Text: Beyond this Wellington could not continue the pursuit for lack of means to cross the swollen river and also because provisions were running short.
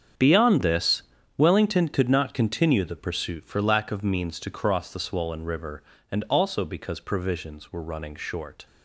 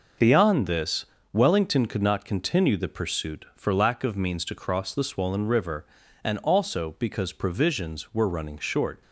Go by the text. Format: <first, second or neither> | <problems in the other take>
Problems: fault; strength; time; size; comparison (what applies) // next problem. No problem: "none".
second | gets quieter; strong; throughout; 14 dB // pauses between "this" and "Wellington"; slight; at 1.0 s; 0.36 s long; slight in the second